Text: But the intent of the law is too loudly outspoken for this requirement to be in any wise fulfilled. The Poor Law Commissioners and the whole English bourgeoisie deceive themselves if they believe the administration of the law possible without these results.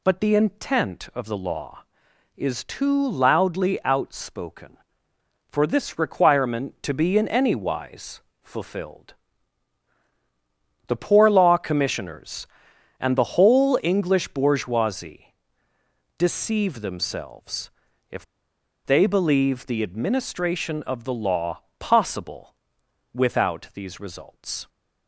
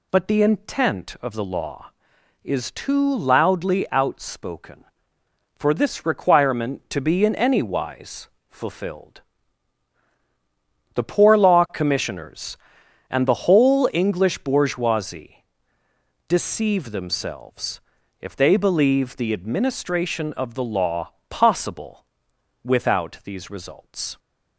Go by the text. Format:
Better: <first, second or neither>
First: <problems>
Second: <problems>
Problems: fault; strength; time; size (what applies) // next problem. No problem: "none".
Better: second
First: pauses between "wise" and "fulfilled"; slight; at 8.2 s; 0.22 s long // pauses between "bourgeoisie" and "deceive"; noticeable; at 15.3 s; 0.84 s long // pauses between "themselves" and "if"; at 17.7 s; 0.40 s long // pauses between "if" and "they"; noticeable; at 18.2 s; 0.61 s long // pauses between "law" and "possible"; slight; at 21.6 s; 0.16 s long // pauses between "possible" and "without"; noticeable; at 22.5 s; 0.58 s long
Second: pauses between "wise" and "fulfilled"; slight; at 8.2 s; 0.22 s long // pauses between "bourgeoisie" and "deceive"; noticeable; at 15.4 s; 0.84 s long // pauses between "themselves" and "if"; at 17.8 s; 0.40 s long // pauses between "law" and "possible"; slight; at 21.1 s; 0.16 s long // pauses between "possible" and "without"; noticeable; at 22.0 s; 0.58 s long